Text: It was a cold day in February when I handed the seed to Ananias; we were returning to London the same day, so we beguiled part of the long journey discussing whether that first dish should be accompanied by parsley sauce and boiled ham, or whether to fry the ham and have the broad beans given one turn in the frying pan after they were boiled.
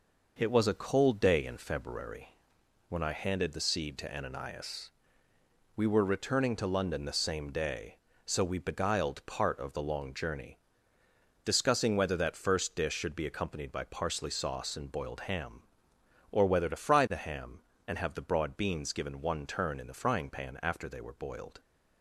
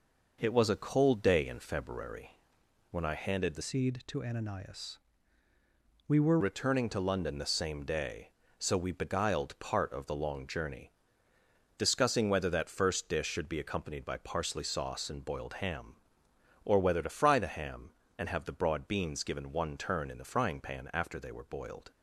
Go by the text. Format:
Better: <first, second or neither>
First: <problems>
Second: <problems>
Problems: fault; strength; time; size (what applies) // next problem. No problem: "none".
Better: first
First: pauses between "February" and "when"; noticeable; at 2.3 s; 0.54 s long // pauses between "journey" and "discussing"; noticeable; at 10.5 s; 0.84 s long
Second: pauses between "February" and "when"; noticeable; at 2.3 s; 0.54 s long // changes voice from "seed" to "were"; from 3.6 to 6.3 s; 2.7 s long // pauses between "journey" and "discussing"; noticeable; at 10.9 s; 0.84 s long